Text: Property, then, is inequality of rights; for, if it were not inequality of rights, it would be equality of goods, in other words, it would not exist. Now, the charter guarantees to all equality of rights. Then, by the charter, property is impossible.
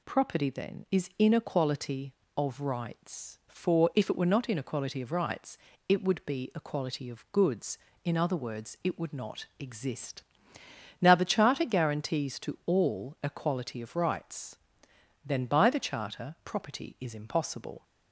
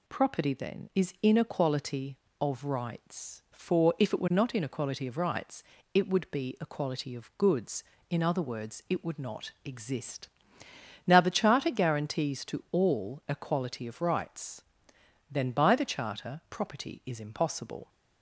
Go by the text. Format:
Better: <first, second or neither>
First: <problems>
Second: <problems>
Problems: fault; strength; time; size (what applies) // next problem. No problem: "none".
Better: neither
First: none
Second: none